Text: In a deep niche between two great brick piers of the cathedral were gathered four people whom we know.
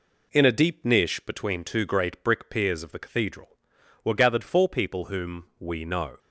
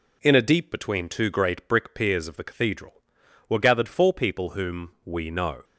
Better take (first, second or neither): first